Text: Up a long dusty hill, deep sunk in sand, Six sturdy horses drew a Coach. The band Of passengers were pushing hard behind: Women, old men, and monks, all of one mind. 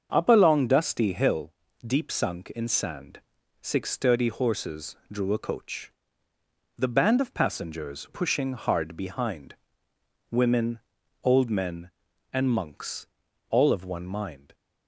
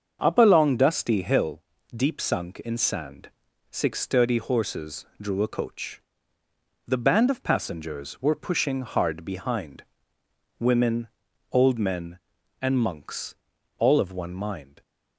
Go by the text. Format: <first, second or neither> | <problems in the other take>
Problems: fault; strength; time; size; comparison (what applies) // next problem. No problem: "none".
second | starts louder than the rest; until 1.1 s; 7 dB; also in the second // skips "were"; at 8.0 s